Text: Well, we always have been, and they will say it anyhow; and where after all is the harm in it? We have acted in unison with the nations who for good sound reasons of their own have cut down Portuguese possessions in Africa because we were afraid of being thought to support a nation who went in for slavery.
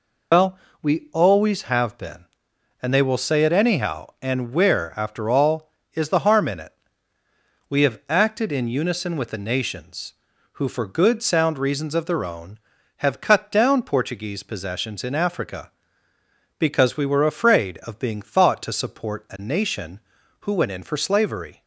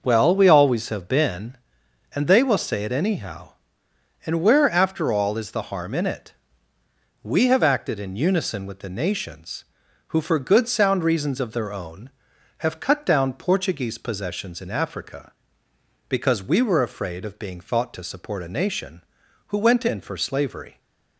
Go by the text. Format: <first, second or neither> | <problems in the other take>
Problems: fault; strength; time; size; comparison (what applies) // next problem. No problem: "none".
second | loses the start of "Well"; at 0.3 s; 95 ms